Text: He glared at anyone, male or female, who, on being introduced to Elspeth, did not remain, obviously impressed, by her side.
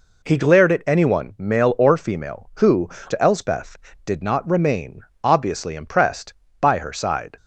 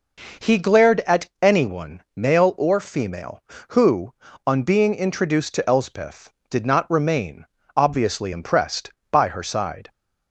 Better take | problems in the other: second | skips "on being introduced"; at 2.9 s

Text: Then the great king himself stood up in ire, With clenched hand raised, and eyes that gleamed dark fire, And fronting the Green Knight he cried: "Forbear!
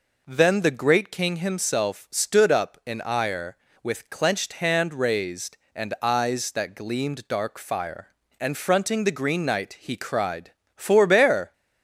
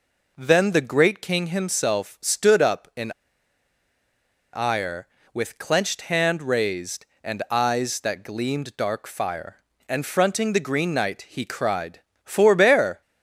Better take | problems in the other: first | pauses between "in" and "ire"; strong; at 3.1 s; 1.4 s long

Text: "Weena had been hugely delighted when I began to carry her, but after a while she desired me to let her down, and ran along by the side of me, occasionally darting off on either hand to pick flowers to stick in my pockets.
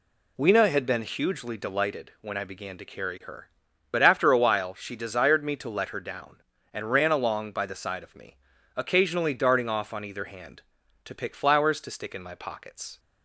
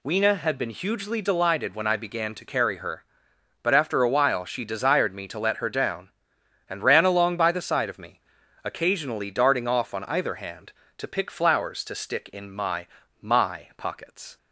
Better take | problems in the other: first | says "my" twice; at 13.2 s

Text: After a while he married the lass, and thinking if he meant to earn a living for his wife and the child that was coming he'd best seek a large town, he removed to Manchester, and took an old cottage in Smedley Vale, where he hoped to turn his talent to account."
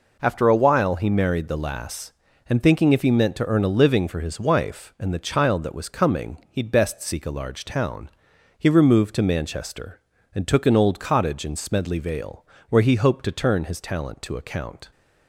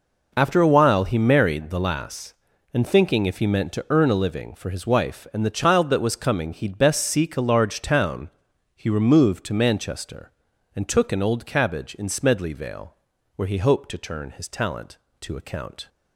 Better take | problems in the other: first | says "cabbage" for "cottage"; at 11.4 s

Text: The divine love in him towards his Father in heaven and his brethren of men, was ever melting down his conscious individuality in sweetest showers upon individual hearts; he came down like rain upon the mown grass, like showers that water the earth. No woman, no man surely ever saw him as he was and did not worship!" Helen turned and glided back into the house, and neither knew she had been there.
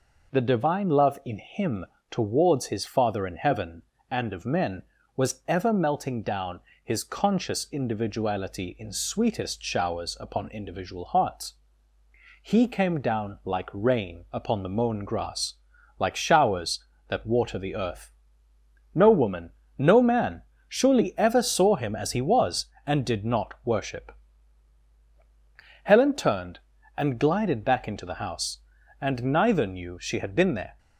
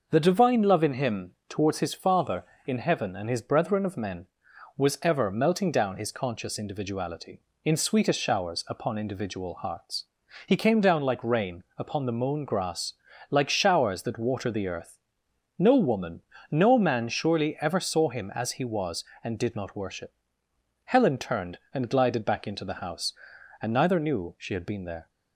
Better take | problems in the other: second | pauses between "him" and "towards"; slight; at 1.8 s; 0.24 s long; slight in the second // skips "his brethren"; at 4.3 s // pauses between "down" and "his"; slight; at 6.5 s; 0.24 s long // pauses between "man" and "surely"; slight; at 20.4 s; 0.26 s long

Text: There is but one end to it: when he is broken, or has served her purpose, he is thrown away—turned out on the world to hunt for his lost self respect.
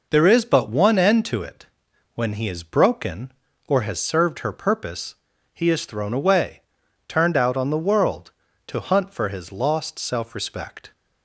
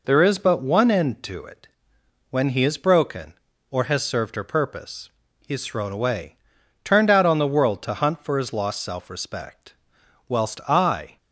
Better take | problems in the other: first | goes on to say "Whilst I"; noticeable; from 10.2 s on; 0.90 s long

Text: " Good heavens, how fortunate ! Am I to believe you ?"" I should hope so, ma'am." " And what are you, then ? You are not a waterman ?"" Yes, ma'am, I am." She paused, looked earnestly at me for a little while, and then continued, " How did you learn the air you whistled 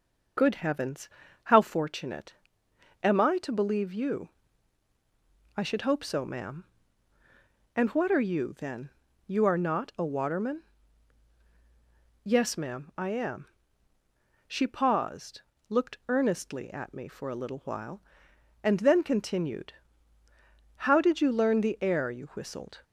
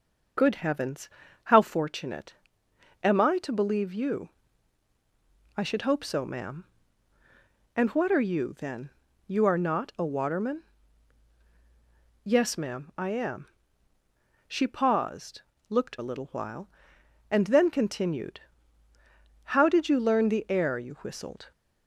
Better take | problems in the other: first | starts louder than the rest; strong; until 1.7 s; 8 dB; strong in the first // skips "earnestly at me for"; at 15.9 s

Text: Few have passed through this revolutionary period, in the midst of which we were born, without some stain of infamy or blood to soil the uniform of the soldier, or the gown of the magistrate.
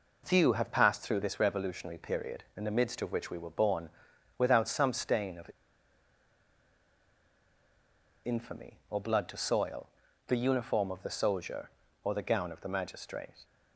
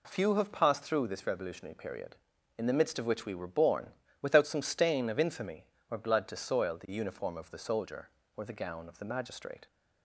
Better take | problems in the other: second | pauses between "of" and "infamy"; strong; at 5.5 s; 2.7 s long // pauses between "soil" and "the"; at 9.8 s; 0.42 s long

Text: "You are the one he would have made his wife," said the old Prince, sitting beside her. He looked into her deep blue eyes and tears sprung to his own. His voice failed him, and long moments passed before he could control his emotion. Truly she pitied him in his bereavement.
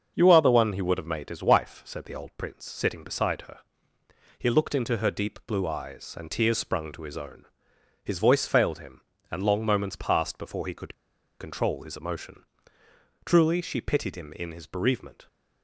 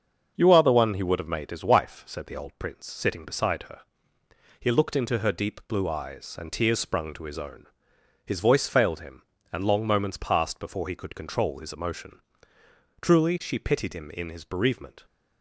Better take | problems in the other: second | starts louder than the rest; until 1.1 s; 6.5 dB; also in the second // pauses between "could" and "control"; noticeable; at 10.9 s; 0.46 s long

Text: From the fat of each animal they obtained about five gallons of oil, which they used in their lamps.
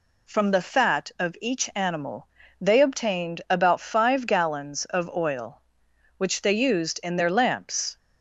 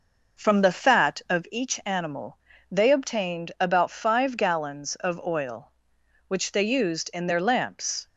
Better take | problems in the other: first | starts louder than the rest; noticeable; until 1.5 s; 5.5 dB // pauses between "animal" and "they"; slight; at 2.3 s; 0.34 s long; slight in the first

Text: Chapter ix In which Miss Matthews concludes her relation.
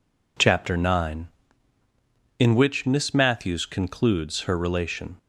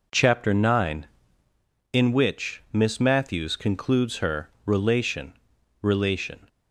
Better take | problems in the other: first | says "relation" twice; at 5.8 s

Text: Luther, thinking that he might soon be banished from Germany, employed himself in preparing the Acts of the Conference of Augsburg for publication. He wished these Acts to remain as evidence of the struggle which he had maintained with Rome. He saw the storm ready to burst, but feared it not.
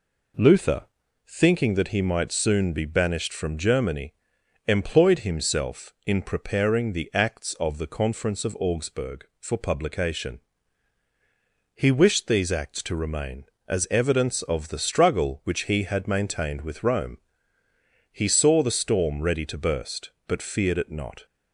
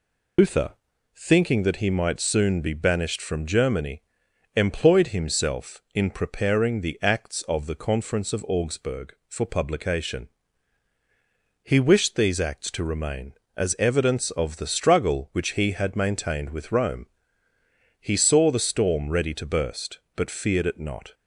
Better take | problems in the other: first | loses the start of "Luther"; at 0.3 s; 140 ms

